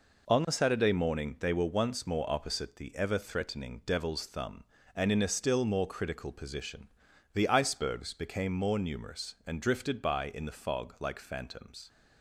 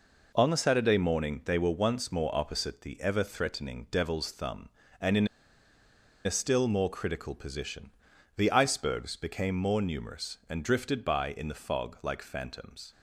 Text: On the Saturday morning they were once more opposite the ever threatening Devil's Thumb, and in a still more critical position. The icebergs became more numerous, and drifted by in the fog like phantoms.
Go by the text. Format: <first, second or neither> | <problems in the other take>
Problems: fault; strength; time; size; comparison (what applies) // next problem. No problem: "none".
first | pauses between "in" and "a"; noticeable; at 5.2 s; 0.97 s long